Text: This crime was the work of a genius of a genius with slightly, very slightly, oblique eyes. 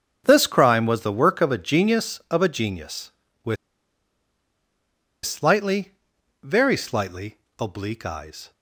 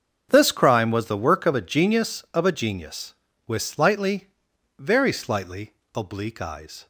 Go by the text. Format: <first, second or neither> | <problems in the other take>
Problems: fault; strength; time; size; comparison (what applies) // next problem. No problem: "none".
second | starts louder than the rest; until 1.2 s; 6.5 dB; also in the second // pauses between "with" and "slightly"; strong; at 3.5 s; 1.7 s long